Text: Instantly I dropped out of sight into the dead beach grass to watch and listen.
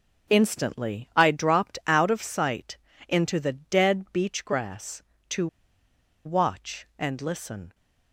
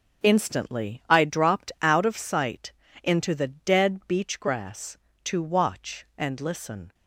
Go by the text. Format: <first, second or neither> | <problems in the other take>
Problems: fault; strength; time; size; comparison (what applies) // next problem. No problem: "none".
second | pauses between "sight" and "into"; slight; at 2.7 s; 0.30 s long; slight in the second // pauses between "to" and "watch"; noticeable; at 5.4 s; 0.78 s long